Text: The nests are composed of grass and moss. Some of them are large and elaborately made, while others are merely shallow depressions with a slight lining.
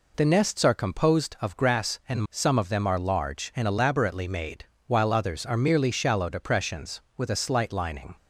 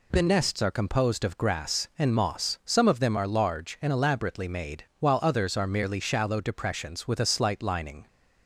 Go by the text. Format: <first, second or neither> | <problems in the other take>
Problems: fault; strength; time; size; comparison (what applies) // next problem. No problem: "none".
second | skips "moss"; at 2.2 s